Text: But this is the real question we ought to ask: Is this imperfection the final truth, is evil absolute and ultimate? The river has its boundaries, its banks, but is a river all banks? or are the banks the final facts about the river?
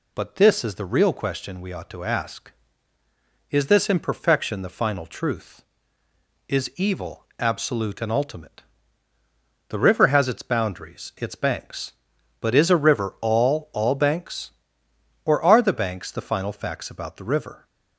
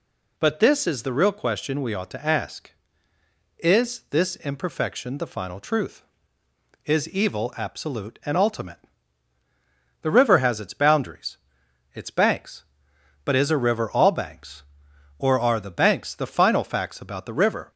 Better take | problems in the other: second | says "all" twice; at 13.7 s

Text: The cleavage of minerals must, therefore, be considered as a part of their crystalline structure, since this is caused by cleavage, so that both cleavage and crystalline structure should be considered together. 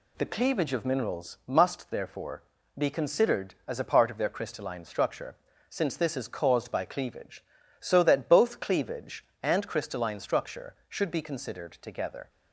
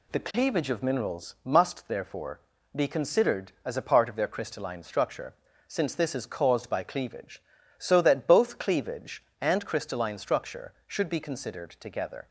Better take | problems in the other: neither | none

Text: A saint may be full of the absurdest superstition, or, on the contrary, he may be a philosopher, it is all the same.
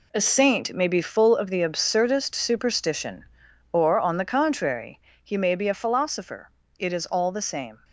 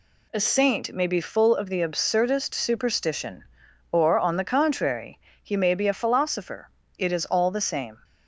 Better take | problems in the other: second | gets quieter; strong; throughout; 8.5 dB

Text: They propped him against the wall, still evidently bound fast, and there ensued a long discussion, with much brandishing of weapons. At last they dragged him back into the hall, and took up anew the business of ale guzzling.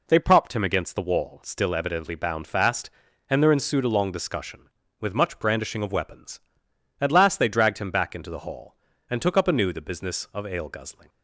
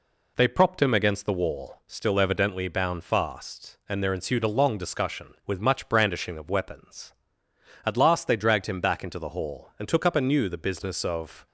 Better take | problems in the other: first | stops before "ale guzzling"; at 11.4 s

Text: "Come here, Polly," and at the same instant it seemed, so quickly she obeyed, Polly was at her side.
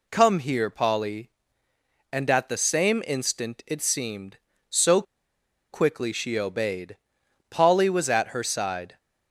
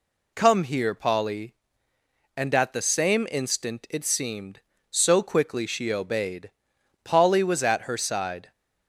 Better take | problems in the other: second | pauses between "so" and "quickly"; noticeable; at 5.0 s; 0.70 s long

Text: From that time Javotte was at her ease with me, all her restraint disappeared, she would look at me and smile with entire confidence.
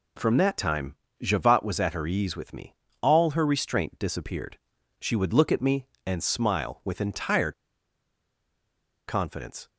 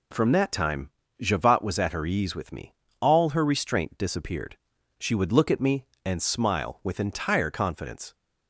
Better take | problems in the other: second | pauses between "time" and "Javotte"; slight; at 0.9 s; 0.28 s long; slight in the second // pauses between "entire" and "confidence"; strong; at 7.5 s; 1.5 s long

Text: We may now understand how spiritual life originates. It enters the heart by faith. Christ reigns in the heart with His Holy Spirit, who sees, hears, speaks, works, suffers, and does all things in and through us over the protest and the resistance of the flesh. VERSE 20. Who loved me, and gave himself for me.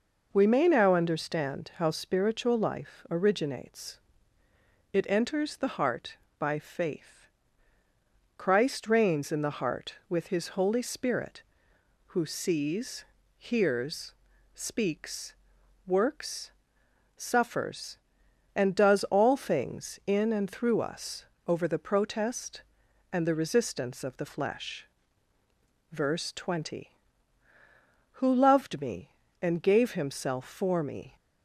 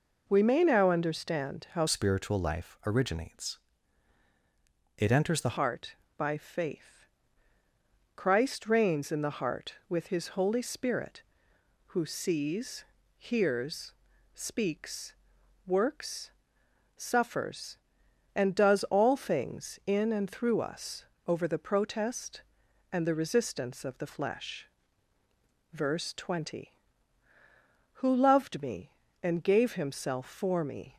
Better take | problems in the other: first | changes voice from "spiritual" to "the"; from 1.8 to 5.5 s; 3.7 s long // pauses between "us" and "over"; slight; at 21.0 s; 0.22 s long; slight in the first

